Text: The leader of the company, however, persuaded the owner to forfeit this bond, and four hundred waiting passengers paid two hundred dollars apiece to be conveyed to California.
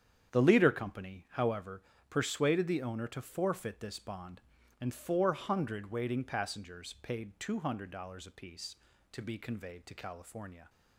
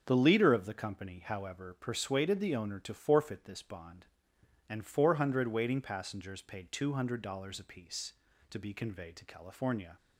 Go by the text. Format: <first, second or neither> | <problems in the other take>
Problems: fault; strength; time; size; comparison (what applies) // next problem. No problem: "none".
second | starts louder than the rest; strong; until 1.3 s; 8.5 dB; also in the second // skips "of the"; at 0.6 s